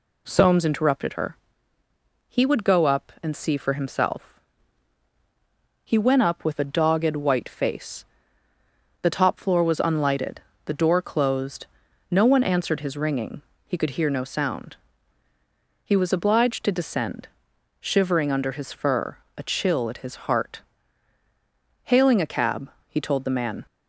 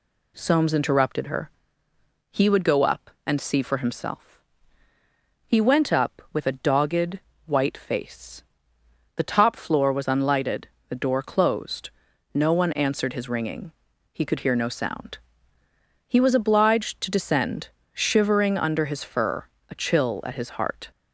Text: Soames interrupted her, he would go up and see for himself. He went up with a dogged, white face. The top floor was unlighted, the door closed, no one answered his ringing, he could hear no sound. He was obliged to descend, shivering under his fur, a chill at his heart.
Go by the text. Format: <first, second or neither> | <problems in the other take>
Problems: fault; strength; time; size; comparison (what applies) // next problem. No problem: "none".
second | goes on to say "Hailing a cab he told the man"; strong; from 21.8 s on; 1.8 s long